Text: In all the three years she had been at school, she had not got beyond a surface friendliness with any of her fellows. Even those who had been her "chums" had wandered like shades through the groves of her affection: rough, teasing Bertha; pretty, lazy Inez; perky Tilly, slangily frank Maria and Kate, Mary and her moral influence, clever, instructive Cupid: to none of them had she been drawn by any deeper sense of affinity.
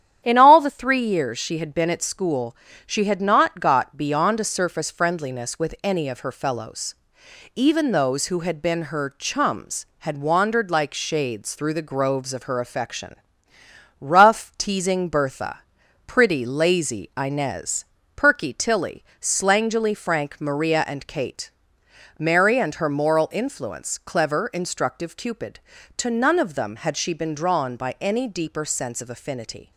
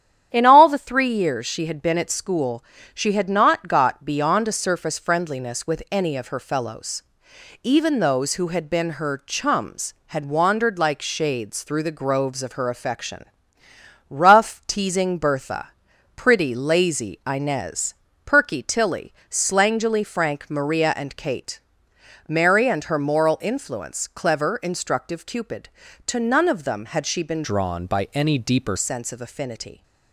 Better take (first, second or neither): first